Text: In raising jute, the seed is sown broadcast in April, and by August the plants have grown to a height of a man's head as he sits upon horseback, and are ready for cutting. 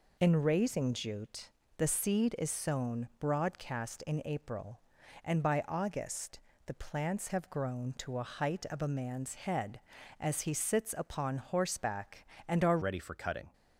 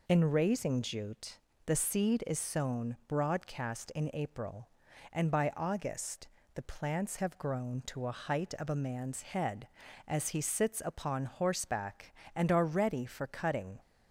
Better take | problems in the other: second | pauses between "August" and "the"; slight; at 6.3 s; 0.26 s long; slight in the second // changes voice at "ready"; from 12.8 s on; 0.7 s long

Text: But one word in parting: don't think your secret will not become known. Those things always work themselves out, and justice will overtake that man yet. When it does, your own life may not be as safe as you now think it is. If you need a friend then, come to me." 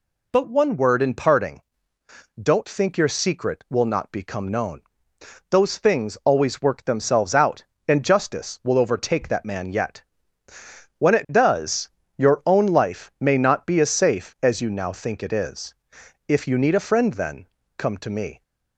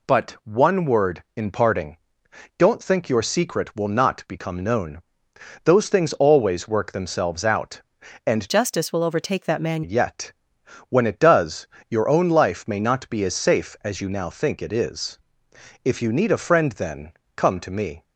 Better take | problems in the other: first | changes voice from "justice" to "man"; from 8.4 to 9.8 s; 1.4 s long

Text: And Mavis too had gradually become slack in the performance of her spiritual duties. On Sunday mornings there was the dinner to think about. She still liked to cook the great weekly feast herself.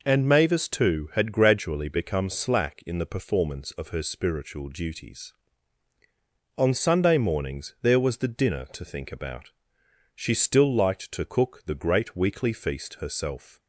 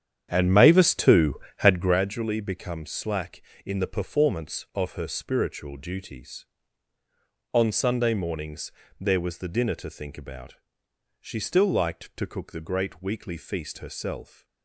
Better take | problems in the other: first | starts louder than the rest; strong; until 2.0 s; 9 dB // pauses between "mornings" and "there"; slight; at 8.7 s; 0.30 s long

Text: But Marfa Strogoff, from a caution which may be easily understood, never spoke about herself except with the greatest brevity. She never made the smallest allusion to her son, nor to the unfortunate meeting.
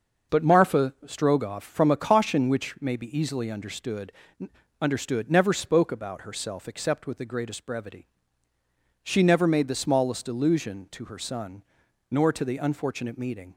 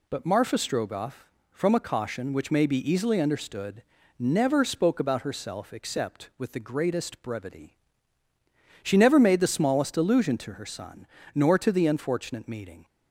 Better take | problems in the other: second | says "understood" twice; at 4.8 s

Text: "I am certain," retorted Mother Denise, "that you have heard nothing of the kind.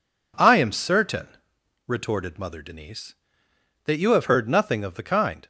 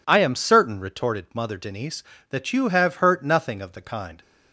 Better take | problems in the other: first | says "hurt" for "heard"; at 2.9 s

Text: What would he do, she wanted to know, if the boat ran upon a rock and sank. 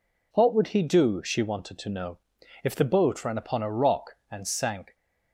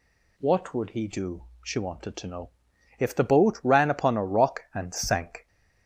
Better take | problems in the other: neither | none

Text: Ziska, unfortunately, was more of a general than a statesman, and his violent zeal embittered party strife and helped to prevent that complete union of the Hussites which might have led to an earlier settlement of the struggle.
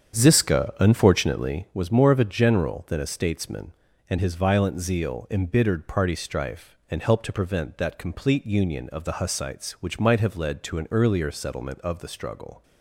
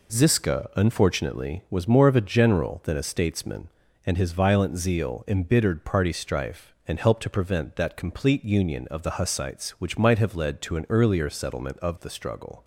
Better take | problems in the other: second | starts louder than the rest; strong; until 1.7 s; 8 dB

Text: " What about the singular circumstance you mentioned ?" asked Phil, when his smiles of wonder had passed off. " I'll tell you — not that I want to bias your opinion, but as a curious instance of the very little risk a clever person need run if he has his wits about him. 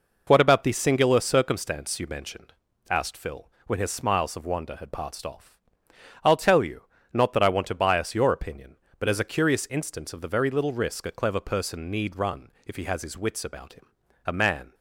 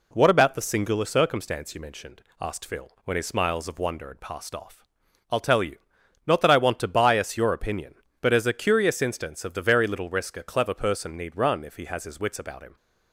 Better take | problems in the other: second | goes on to say "A man"; slight; from 14.2 s on; 0.48 s long

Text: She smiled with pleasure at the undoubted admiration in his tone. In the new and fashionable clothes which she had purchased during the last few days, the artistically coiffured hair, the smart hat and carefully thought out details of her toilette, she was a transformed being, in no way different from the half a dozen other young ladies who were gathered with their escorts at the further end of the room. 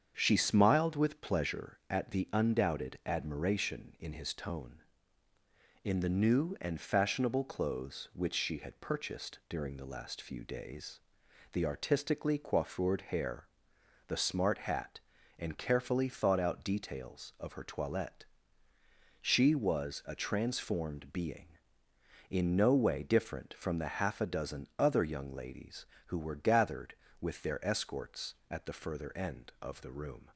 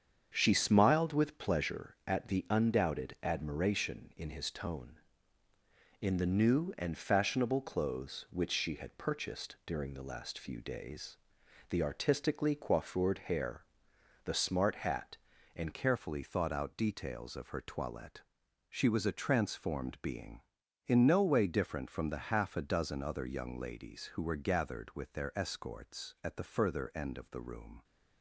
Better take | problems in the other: first | starts louder than the rest; strong; until 1.3 s; 7.5 dB; strong in the first // changes voice at "carefully"; from 15.7 s on; 12.1 s long

